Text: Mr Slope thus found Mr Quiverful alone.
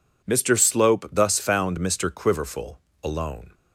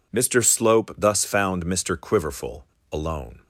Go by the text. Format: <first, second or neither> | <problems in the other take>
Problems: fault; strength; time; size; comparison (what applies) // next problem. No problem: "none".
neither | pauses between "Quiverful" and "alone"; slight; the same in both